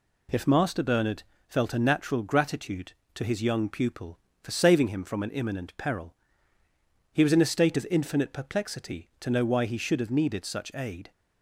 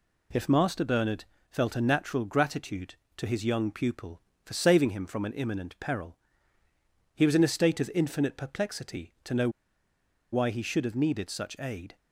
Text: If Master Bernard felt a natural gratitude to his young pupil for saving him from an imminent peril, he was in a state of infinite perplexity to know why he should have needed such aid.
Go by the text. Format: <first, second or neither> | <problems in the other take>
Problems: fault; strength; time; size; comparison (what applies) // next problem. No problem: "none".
first | pauses between "Bernard" and "felt"; slight; at 1.2 s; 0.24 s long; slight in the first // pauses between "know" and "why"; noticeable; at 9.4 s; 0.82 s long